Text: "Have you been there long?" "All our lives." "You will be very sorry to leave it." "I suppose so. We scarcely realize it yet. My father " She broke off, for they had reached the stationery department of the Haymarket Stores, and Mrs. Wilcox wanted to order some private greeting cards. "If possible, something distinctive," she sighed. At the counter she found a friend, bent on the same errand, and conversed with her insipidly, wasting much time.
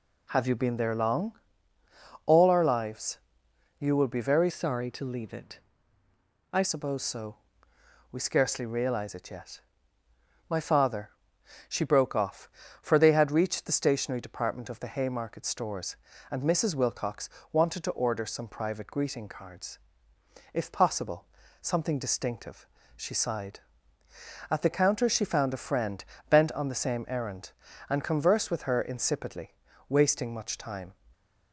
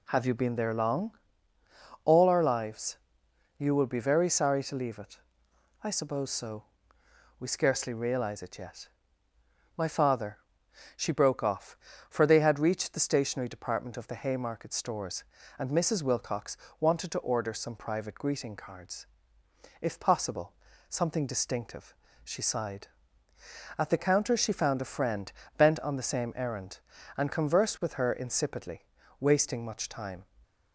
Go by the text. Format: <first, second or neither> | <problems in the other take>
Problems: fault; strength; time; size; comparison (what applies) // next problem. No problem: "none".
second | changes voice from "sorry" to "I"; from 4.4 to 6.6 s; 2.2 s long // pauses between "Wilcox" and "wanted"; slight; at 17.2 s; 0.24 s long; slight in the second